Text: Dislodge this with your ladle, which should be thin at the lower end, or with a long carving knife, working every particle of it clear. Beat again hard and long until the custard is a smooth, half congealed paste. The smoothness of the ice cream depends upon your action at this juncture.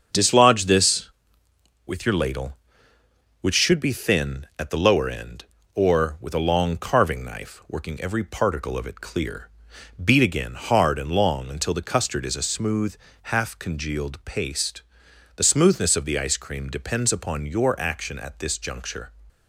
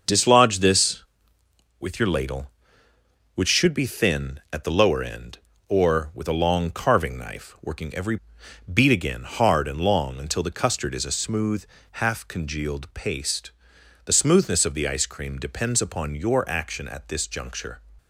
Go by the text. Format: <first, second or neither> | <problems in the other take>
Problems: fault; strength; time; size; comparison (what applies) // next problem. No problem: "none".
first | starts louder than the rest; until 1.8 s; 6.5 dB; also in the first // skips "particle of it clear"; at 8.4 s